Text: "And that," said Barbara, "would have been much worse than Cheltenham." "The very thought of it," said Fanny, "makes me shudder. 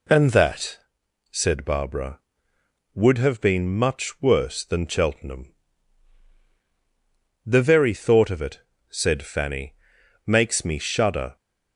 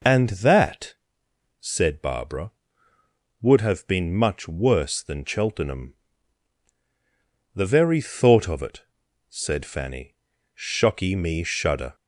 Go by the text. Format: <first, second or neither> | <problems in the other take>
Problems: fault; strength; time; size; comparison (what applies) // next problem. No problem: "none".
first | says "shocky" for "makes"; at 10.5 s